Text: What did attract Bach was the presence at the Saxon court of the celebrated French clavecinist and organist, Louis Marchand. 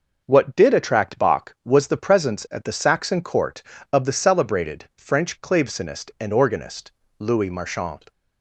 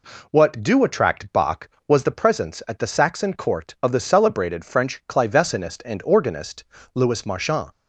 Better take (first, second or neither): first